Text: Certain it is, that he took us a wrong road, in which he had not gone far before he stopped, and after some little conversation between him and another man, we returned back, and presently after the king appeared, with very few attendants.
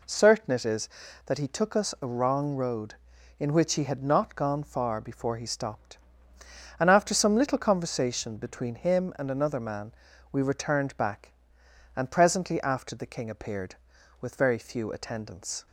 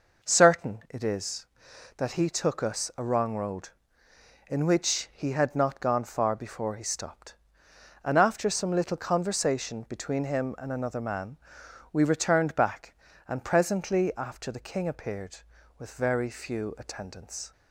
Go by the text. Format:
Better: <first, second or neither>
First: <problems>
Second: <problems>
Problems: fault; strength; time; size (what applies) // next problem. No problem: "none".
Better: neither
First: none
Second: none